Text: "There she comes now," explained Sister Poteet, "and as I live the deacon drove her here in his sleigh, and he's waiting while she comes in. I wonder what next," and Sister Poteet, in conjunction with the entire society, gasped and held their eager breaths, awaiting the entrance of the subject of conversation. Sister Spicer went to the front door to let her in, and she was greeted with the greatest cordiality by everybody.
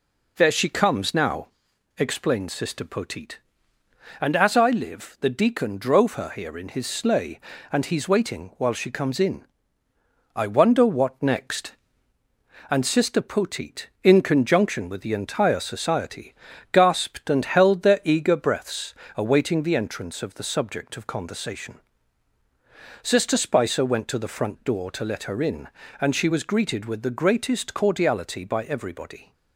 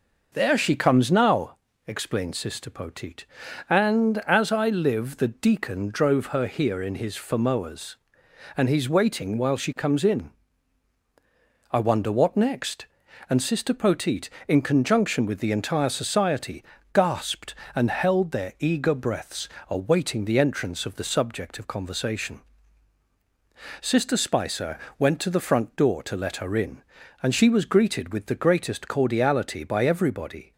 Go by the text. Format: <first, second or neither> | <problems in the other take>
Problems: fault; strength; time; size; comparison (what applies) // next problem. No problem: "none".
first | says "famoas" for "sleigh"; at 7.1 s // pauses between "Spicer" and "went"; slight; at 24.7 s; 0.20 s long